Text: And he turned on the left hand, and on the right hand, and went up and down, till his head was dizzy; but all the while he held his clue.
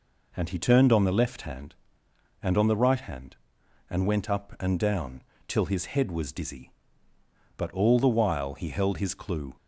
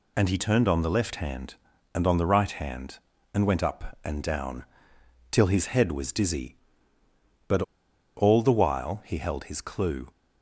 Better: first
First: none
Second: pauses between "but" and "all"; noticeable; at 7.6 s; 0.55 s long

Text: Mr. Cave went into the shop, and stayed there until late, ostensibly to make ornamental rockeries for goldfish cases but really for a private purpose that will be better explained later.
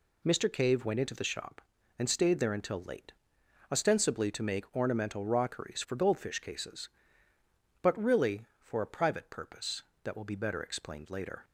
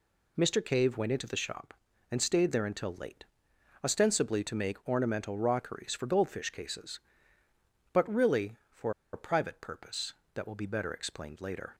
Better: first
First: none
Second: pauses between "for" and "a"; slight; at 8.9 s; 0.22 s long

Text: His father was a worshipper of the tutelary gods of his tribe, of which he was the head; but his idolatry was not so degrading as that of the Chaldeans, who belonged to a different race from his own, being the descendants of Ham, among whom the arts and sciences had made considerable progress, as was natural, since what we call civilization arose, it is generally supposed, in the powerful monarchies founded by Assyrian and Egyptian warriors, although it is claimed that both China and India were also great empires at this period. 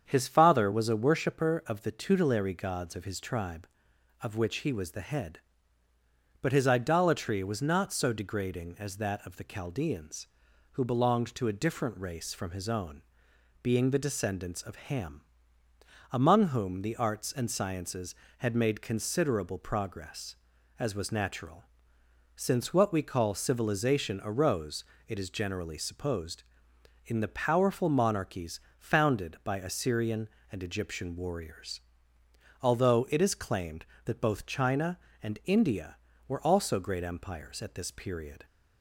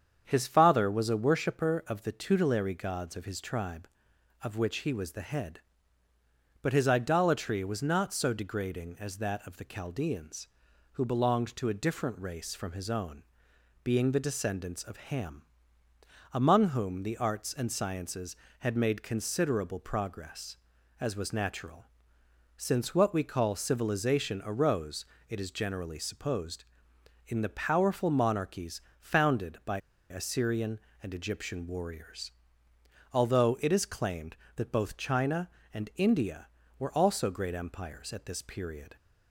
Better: first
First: starts louder than the rest; strong; until 1.0 s; 8 dB // pauses between "monarchies" and "founded"; slight; at 28.5 s; 0.20 s long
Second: starts louder than the rest; strong; until 1.2 s; 8 dB // pauses between "monarchies" and "founded"; slight; at 28.7 s; 0.20 s long // pauses between "by" and "Assyrian"; slight; at 29.7 s; 0.32 s long

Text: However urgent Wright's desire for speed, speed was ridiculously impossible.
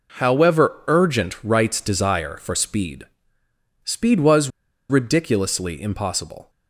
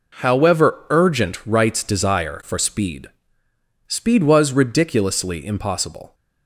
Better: second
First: pauses between "was" and "ridiculously"; at 4.4 s; 0.40 s long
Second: none

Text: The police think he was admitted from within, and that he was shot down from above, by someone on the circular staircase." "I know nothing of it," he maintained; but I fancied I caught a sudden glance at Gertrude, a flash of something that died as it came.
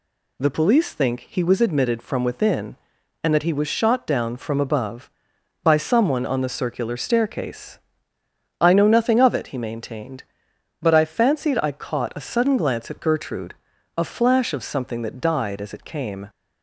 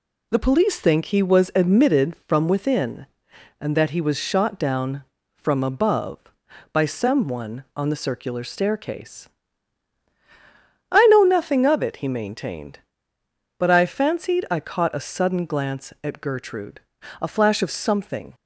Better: first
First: none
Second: stops before "that died as it came"; at 18.3 s

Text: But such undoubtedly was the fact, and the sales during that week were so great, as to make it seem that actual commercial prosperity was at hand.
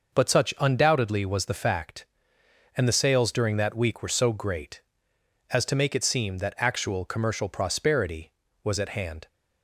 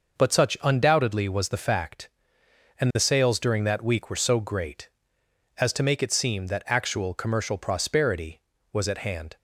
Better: neither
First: none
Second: none

